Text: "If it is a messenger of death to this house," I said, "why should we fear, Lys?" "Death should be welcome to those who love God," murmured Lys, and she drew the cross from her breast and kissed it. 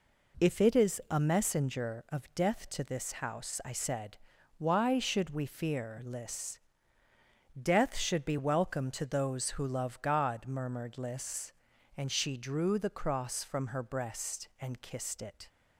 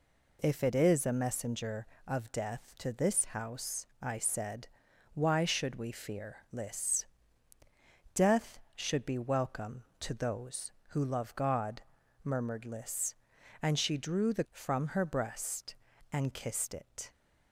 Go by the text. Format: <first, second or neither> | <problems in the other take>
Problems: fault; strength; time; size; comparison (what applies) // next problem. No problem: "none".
first | skips "cross"; at 14.4 s